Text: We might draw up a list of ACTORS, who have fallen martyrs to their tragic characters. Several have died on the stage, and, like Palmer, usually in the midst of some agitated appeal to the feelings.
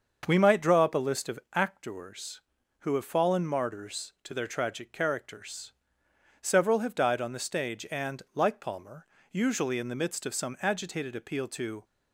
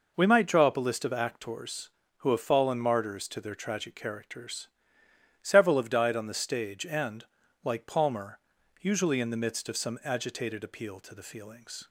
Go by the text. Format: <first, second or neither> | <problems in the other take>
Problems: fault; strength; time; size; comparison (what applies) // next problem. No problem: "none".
second | starts louder than the rest; until 1.2 s; 6.5 dB // pauses between "of" and "ACTORS"; slight; at 1.3 s; 0.16 s long // stops before "the feelings"; at 11.8 s